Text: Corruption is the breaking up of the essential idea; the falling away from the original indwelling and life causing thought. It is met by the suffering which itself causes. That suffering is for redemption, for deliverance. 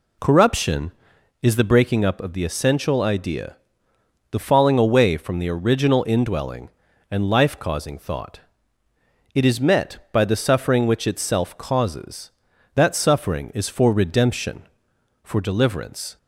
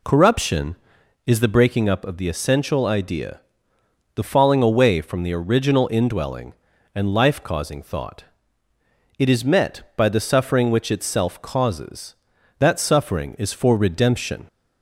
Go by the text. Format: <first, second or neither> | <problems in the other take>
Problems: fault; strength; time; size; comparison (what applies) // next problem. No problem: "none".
first | stops before "for deliverance"; at 14.4 s